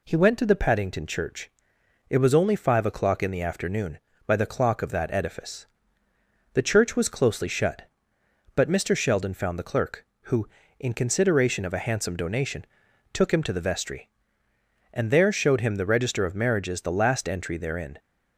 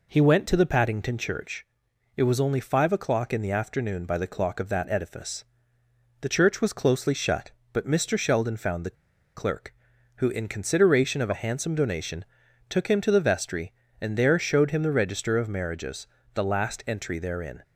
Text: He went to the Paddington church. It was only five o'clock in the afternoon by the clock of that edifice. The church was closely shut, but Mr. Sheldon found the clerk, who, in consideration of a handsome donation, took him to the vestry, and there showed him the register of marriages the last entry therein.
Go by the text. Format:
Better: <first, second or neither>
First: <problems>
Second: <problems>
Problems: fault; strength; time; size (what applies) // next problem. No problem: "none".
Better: first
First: none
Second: pauses between "the" and "clerk"; at 8.9 s; 0.42 s long // pauses between "marriages" and "the"; slight; at 16.0 s; 0.26 s long